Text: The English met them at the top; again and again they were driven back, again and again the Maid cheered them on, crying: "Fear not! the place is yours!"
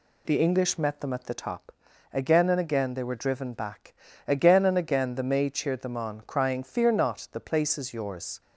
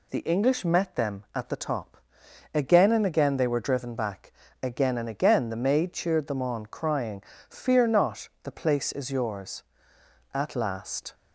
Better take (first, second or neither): first